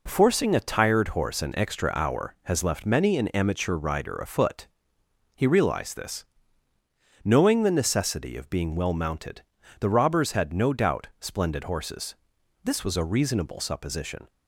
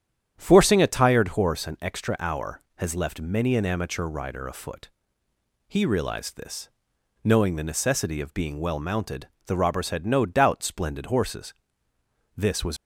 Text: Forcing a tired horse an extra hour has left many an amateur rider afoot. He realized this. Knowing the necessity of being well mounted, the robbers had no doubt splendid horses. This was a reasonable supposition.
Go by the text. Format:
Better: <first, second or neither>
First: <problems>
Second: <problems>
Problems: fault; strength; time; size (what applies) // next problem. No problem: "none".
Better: first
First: none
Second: starts louder than the rest; strong; until 1.3 s; 9.5 dB // stops before "a reasonable supposition"; at 12.7 s